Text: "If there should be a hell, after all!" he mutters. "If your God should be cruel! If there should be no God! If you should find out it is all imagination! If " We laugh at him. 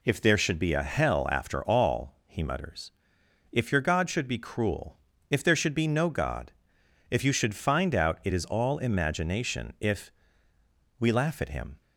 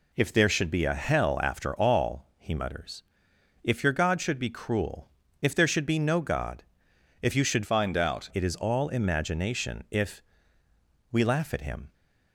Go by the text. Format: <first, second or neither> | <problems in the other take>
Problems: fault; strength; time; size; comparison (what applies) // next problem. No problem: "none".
first | changes voice from "find" to "out"; from 7.6 to 8.2 s; 0.6 s long